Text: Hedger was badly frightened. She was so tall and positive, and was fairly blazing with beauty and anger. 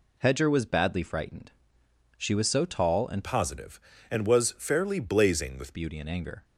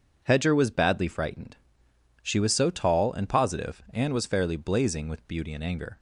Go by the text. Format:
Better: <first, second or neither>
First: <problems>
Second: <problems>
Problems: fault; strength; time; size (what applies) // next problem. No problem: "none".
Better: second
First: changes voice from "positive" to "with"; from 3.2 to 5.7 s; 2.5 s long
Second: none